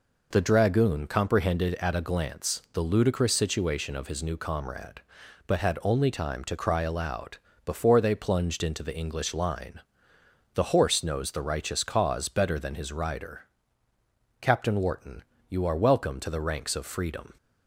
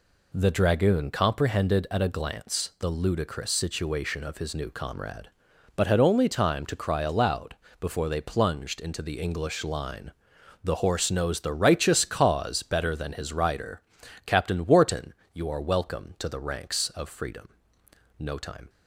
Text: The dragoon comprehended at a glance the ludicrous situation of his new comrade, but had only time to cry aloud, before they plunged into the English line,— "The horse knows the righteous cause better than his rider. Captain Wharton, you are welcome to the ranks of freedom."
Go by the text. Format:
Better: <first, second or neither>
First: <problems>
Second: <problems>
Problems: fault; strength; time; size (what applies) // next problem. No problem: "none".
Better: first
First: none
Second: goes on to say "No time"; from 18.1 s on; 0.52 s long